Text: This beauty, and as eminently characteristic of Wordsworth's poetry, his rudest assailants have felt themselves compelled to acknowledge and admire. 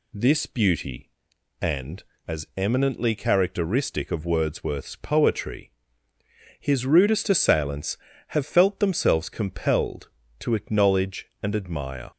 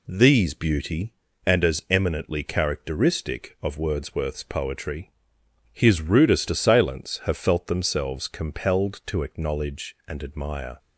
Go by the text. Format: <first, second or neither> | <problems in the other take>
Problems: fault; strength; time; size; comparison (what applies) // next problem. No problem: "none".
first | says "These" for "This"; at 0.0 s